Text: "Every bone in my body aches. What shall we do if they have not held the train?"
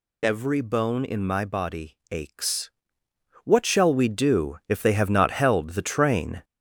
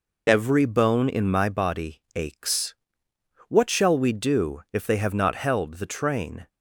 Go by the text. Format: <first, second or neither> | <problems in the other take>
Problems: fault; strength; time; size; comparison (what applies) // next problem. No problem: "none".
second | gets louder; noticeable; throughout; 5 dB